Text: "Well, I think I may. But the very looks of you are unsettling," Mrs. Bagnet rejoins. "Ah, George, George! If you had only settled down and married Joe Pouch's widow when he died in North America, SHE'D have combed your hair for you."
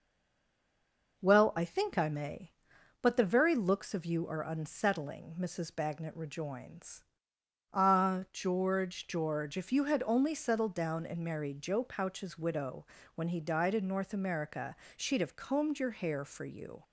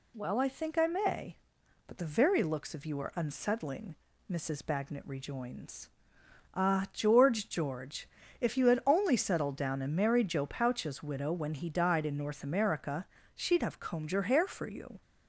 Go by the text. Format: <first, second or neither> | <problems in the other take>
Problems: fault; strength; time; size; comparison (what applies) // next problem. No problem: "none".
second | stays silent before the first word; noticeable; until 1.1 s; 1.1 s long // pauses between "widow" and "when"; slight; at 12.8 s; 0.30 s long